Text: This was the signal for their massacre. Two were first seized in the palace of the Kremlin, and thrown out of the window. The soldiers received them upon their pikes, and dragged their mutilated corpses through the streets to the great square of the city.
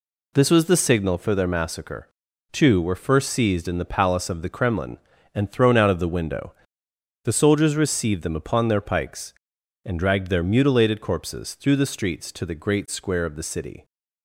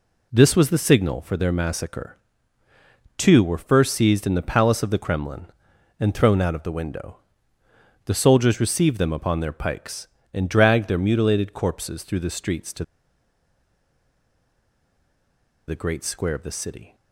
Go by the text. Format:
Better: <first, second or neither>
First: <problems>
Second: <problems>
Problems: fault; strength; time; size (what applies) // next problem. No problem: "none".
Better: first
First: none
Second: pauses between "to" and "the"; strong; at 12.8 s; 2.8 s long